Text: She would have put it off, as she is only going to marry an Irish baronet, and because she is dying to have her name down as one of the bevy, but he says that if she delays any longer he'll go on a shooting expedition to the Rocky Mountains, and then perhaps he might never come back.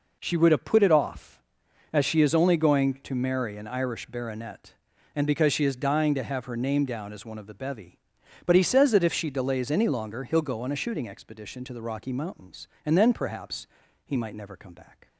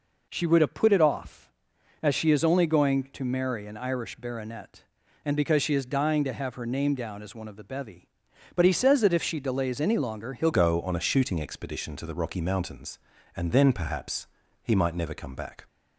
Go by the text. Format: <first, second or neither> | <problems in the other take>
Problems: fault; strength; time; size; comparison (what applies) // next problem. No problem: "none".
first | changes voice at "go"; from 10.5 s on; 5.1 s long // pauses between "perhaps" and "he"; slight; at 14.2 s; 0.36 s long; also in the first